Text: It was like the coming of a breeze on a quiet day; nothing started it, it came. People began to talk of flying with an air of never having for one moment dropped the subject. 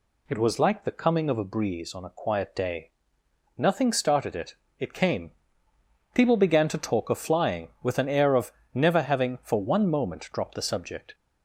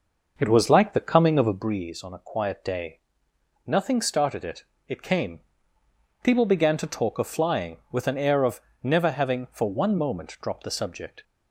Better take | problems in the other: first | starts louder than the rest; noticeable; until 1.7 s; 6 dB // pauses between "of" and "never"; slight; at 8.6 s; 0.22 s long; slight in the first

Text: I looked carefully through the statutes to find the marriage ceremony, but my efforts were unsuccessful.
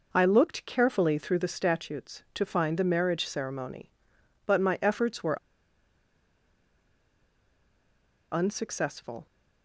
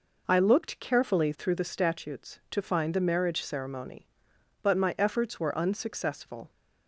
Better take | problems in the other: second | pauses between "were" and "unsuccessful"; strong; at 5.3 s; 2.9 s long

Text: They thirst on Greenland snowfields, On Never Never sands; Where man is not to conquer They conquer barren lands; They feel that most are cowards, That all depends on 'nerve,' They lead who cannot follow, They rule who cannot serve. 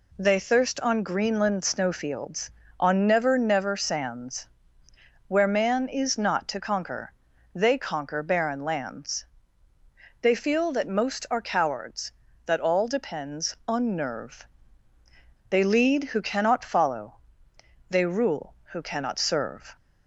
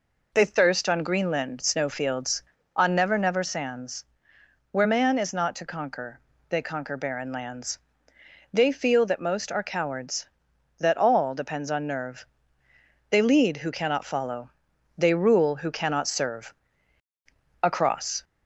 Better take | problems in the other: first | pauses between "conquer" and "They"; slight; at 6.1 s; 0.30 s long; also in the first // goes on to say "Across"; noticeable; from 17.6 s on; 0.62 s long

